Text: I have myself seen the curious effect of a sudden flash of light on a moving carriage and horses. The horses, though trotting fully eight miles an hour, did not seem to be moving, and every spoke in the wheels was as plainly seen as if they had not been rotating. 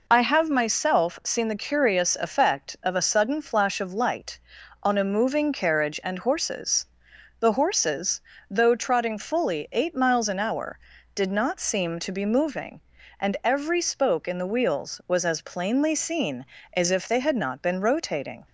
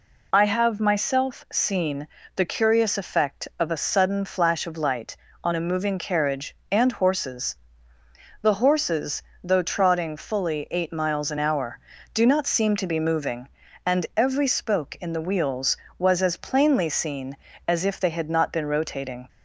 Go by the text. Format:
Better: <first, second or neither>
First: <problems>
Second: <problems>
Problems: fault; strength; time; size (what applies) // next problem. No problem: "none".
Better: first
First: none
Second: pauses between "seen" and "the"; slight; at 2.0 s; 0.26 s long // says "do" for "did"; at 12.1 s